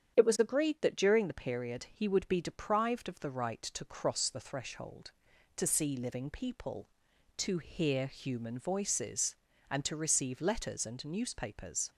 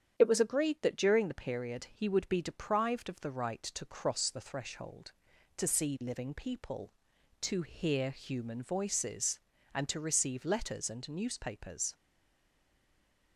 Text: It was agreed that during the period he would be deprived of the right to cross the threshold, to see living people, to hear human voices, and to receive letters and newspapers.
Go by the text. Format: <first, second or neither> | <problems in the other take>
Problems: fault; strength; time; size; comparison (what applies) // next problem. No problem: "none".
first | starts louder than the rest; strong; until 1.1 s; 8.5 dB; strong in the first // stays silent after the last word; noticeable; from 11.9 s on; 1.4 s long